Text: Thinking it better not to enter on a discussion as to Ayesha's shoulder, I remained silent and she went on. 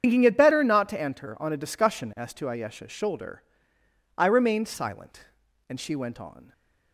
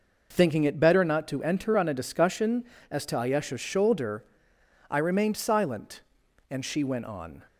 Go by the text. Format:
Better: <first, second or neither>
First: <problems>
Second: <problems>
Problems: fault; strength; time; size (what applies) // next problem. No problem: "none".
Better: second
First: loses the start of "Thinking"; at 0.0 s; 70 ms // starts louder than the rest; strong; until 1.0 s; 8 dB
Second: none